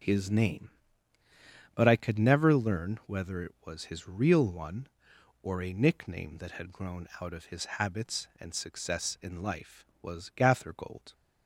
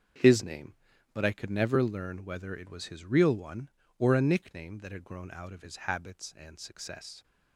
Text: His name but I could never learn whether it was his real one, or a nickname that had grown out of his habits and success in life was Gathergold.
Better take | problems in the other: first | starts louder than the rest; strong; until 1.6 s; 7 dB // stops before "in life was Gathergold"; at 7.2 s

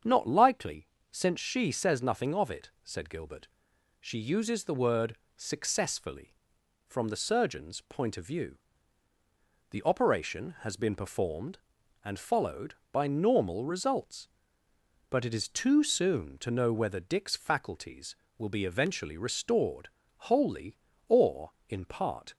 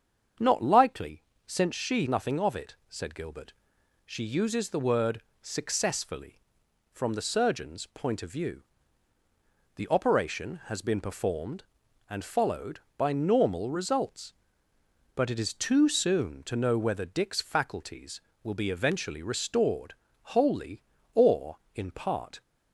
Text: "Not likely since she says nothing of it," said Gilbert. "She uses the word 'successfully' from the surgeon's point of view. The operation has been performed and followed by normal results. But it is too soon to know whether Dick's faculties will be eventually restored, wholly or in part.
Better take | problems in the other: first | starts louder than the rest; strong; until 1.6 s; 7.5 dB; strong in the first // pauses between "likely" and "since"; slight; at 1.2 s; 0.24 s long; slight in the first // skips "says"; at 2.0 s // pauses between "word" and "successfully"; slight; at 5.2 s; 0.18 s long; slight in the first

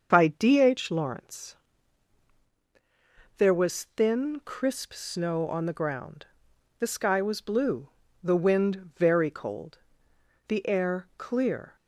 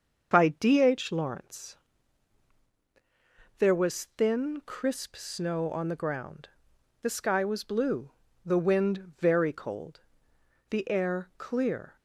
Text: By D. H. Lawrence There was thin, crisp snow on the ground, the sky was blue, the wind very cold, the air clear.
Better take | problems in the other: neither | starts louder than the rest; the same in both // pauses between "Lawrence" and "There"; strong; the same in both

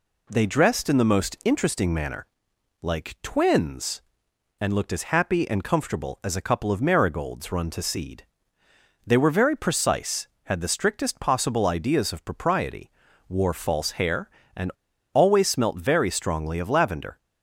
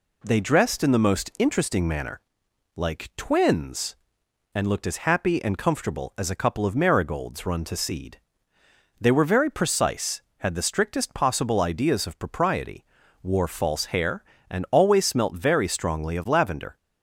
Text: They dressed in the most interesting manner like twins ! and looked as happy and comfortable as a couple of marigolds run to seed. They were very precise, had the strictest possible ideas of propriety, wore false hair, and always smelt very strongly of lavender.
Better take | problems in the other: second | pauses between "manner" and "like"; noticeable; at 2.2 s; 0.54 s long; noticeable in the second // pauses between "and" and "always"; at 14.7 s; 0.42 s long

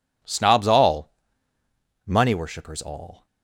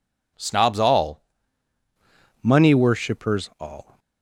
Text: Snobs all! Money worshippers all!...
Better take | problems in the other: first | changes voice at "Money"; from 2.4 s on; 1.5 s long

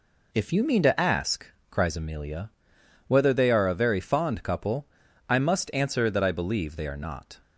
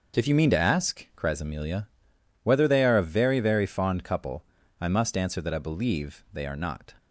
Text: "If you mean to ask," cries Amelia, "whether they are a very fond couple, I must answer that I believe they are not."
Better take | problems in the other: first | starts louder than the rest; until 1.2 s; 6.5 dB // says "very" twice; at 3.4 s

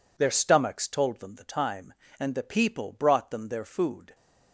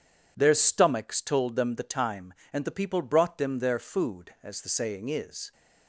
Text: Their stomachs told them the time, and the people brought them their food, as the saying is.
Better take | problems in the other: second | stops before "as the saying is"; at 4.1 s

